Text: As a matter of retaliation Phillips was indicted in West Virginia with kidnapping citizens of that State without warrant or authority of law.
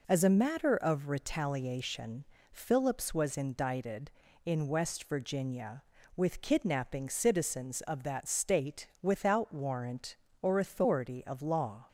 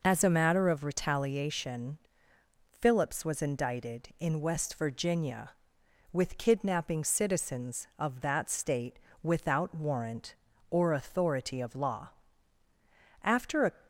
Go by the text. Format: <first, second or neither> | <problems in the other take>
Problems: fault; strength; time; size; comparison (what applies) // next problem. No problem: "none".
first | pauses between "retaliation" and "Phillips"; noticeable; at 1.9 s; 0.72 s long; slight in the first // pauses between "State" and "without"; slight; at 8.9 s; 0.24 s long; slight in the first // goes on to say "After a"; slight; from 13.2 s on; 0.48 s long